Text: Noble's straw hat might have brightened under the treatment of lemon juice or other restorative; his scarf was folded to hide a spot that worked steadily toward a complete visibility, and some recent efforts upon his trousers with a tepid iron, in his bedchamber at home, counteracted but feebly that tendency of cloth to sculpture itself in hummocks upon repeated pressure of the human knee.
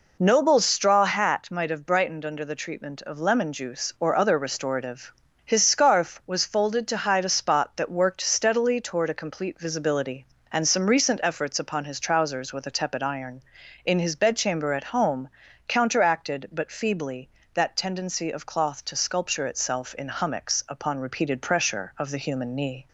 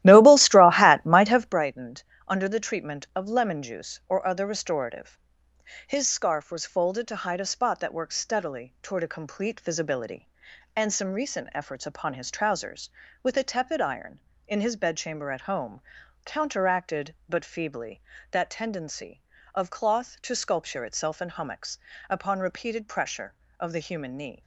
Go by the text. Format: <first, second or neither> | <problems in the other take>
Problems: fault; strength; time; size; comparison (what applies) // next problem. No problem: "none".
first | starts louder than the rest; strong; until 1.7 s; 14.5 dB // pauses between "brightened" and "under"; slight; at 2.0 s; 0.24 s long // pauses between "hummocks" and "upon"; slight; at 21.7 s; 0.32 s long